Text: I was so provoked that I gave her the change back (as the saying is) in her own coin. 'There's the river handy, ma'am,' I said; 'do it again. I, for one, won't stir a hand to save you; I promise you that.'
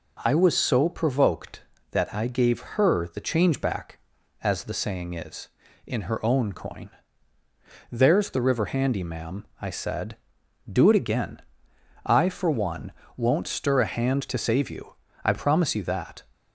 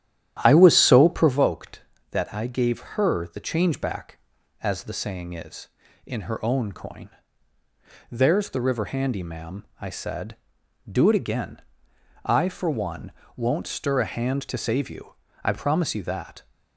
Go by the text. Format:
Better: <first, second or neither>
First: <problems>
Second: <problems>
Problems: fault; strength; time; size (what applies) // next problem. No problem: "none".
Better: first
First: none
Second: starts louder than the rest; strong; until 1.4 s; 11 dB